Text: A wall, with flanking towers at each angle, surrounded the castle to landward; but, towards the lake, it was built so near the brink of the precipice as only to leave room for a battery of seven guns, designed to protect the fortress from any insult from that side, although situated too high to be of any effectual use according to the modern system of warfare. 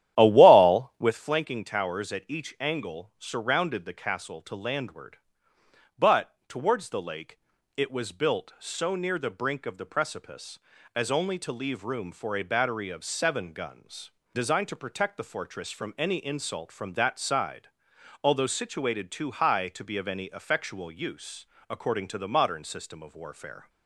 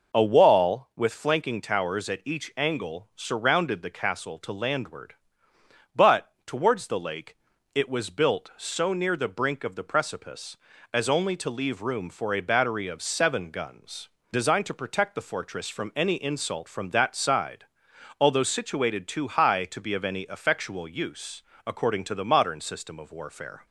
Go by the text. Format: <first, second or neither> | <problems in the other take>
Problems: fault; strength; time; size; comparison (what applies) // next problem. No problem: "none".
second | starts louder than the rest; strong; until 1.1 s; 12 dB // pauses between "use" and "according"; slight; at 21.4 s; 0.24 s long; slight in the second